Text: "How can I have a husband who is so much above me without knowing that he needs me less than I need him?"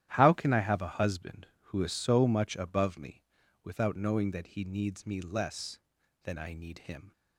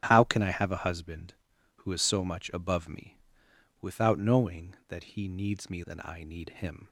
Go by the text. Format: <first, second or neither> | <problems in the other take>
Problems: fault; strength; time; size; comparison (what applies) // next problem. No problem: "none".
first | starts louder than the rest; strong; until 1.0 s; 11.5 dB; strong in the first // pauses between "me" and "without"; noticeable; at 3.1 s; 0.64 s long; also in the first // skips "less"; at 5.8 s